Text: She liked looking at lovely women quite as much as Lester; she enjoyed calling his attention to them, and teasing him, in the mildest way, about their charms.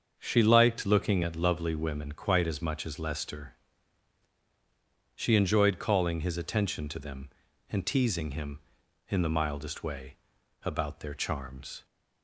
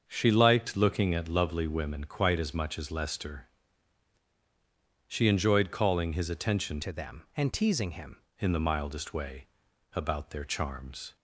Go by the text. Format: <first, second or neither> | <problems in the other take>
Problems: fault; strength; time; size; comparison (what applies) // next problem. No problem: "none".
first | starts louder than the rest; until 1.0 s; 6.5 dB; also in the first // changes voice from "to" to "him"; from 6.8 to 8.1 s; 1.3 s long